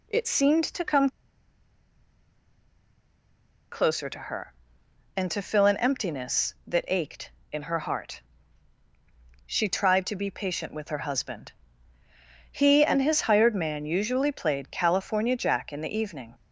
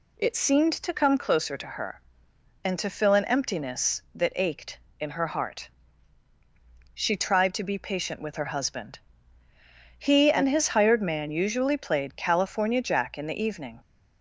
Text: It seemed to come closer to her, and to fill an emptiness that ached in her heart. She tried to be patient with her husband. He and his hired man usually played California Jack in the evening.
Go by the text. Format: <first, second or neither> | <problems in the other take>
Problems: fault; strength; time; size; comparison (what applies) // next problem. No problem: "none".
second | pauses between "come" and "closer"; strong; at 1.0 s; 2.6 s long